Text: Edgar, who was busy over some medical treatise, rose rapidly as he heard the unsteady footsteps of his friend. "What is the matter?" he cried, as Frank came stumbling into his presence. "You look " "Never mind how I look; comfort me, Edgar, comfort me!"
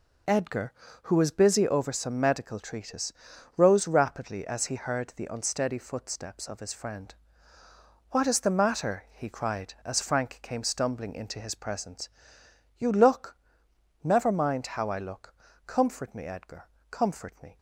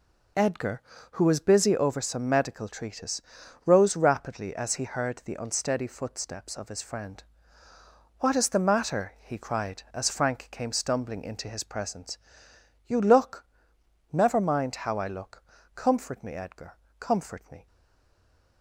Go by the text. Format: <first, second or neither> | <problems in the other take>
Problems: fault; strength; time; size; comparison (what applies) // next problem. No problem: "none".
first | stays silent after the last word; from 17.6 s on; 1.0 s long